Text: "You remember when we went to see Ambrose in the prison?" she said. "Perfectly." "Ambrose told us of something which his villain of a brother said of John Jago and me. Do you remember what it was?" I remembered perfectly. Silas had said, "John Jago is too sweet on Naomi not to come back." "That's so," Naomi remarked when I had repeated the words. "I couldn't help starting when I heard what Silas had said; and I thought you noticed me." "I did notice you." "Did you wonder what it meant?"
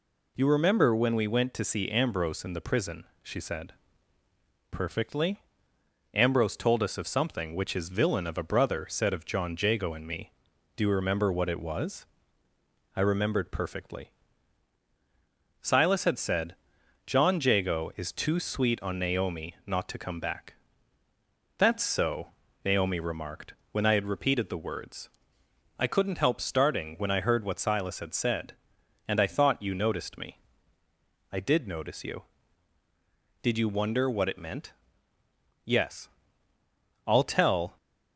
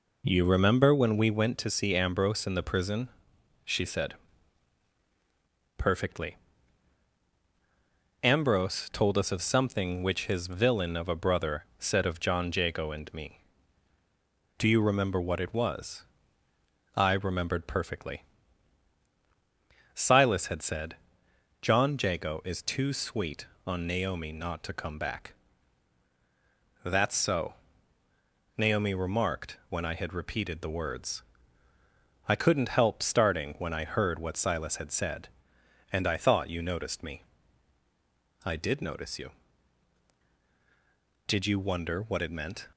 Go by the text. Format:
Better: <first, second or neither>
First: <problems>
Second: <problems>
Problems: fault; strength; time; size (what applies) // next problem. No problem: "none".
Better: second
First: pauses between "remarked" and "when"; slight; at 23.5 s; 0.18 s long // goes on to say "Yes I'll tell"; strong; from 35.6 s on; 2.1 s long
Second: none